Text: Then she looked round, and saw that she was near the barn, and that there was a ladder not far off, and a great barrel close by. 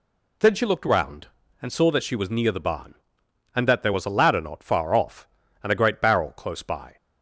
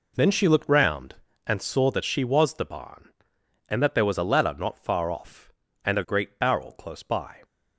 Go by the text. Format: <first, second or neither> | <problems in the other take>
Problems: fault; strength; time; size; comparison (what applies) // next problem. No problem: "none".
first | skips "near"; at 2.5 s